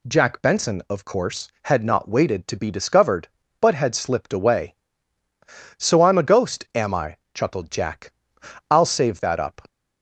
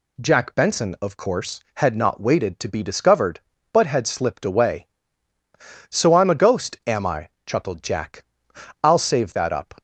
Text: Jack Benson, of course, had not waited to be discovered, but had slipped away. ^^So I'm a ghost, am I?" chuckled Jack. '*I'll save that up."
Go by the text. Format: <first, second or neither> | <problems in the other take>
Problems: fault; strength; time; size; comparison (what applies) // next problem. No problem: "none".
neither | none